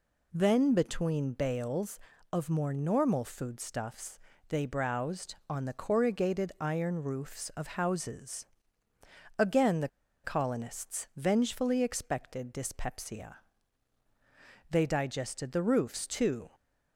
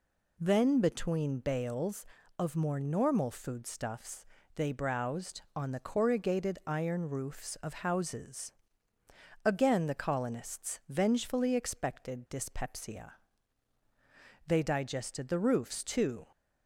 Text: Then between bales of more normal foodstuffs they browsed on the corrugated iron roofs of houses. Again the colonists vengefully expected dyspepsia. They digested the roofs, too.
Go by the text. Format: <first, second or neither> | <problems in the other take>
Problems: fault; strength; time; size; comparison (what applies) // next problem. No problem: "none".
second | pauses between "foodstuffs" and "they"; slight; at 4.1 s; 0.30 s long; slight in the second // pauses between "the" and "colonists"; slight; at 9.8 s; 0.34 s long